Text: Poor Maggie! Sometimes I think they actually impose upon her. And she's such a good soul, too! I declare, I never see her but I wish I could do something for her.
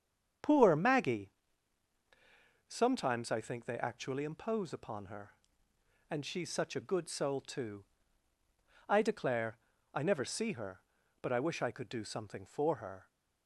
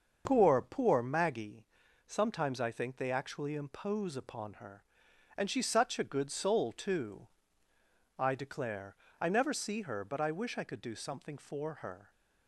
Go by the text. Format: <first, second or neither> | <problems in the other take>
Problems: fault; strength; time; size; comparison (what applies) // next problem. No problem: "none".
first | starts louder than the rest; until 1.2 s; 6.5 dB; strong in the first // says "Poor" twice; at 0.6 s